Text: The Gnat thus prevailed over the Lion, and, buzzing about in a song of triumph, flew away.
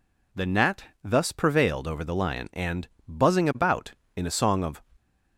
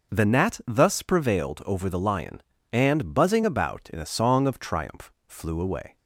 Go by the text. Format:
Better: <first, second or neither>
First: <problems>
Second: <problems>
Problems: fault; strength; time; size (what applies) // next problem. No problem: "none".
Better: second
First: pauses between "Gnat" and "thus"; slight; at 0.8 s; 0.20 s long // stops before "triumph flew away"; at 4.9 s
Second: none